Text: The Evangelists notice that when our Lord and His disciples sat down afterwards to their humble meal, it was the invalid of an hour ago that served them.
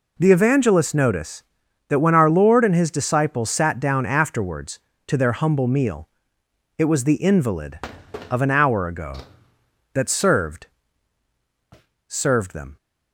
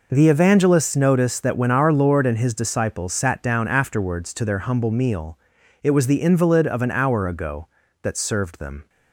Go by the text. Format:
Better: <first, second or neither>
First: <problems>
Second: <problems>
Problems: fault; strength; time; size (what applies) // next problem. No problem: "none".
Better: second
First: says "served" twice; at 12.0 s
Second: none